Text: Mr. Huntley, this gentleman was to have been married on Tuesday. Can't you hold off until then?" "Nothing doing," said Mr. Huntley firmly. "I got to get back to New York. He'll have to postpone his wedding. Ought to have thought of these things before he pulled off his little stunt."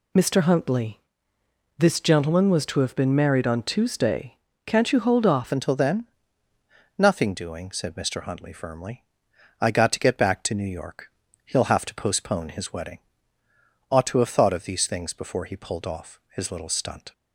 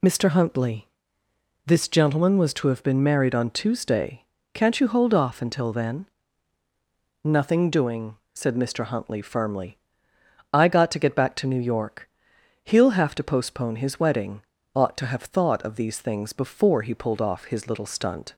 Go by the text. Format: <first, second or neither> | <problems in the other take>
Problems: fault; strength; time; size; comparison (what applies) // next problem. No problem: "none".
second | changes voice at "until"; from 5.5 s on; 11.6 s long // pauses between "off" and "his"; slight; at 16.1 s; 0.16 s long